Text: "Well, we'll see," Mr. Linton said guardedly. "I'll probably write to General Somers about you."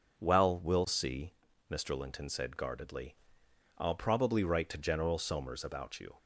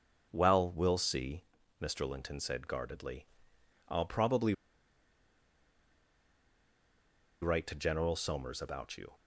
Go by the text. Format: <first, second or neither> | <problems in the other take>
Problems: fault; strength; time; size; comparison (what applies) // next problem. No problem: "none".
first | pauses between "probably" and "write"; strong; at 4.5 s; 2.8 s long